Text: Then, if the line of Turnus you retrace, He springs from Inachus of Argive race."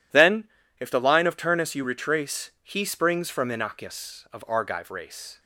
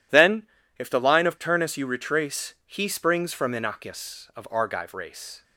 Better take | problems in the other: neither | none

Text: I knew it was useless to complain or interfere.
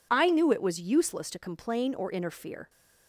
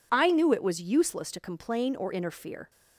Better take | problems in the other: neither | none

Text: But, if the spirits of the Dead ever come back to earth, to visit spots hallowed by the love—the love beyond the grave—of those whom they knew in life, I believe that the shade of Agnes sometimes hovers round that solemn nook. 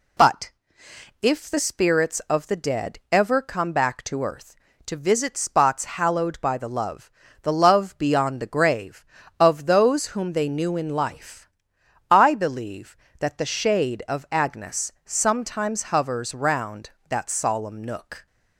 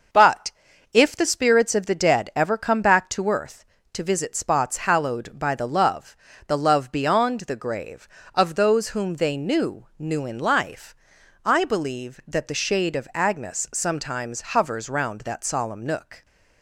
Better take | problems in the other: first | starts louder than the rest; until 1.5 s; 6 dB // says "knew" twice; at 9.9 s

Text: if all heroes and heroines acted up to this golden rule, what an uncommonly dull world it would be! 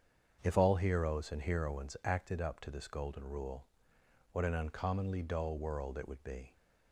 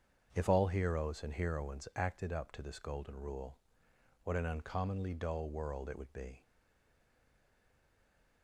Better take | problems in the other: first | starts louder than the rest; strong; until 1.3 s; 7.5 dB; strong in the first // stays silent after the last word; noticeable; from 6.4 s on; 2.0 s long

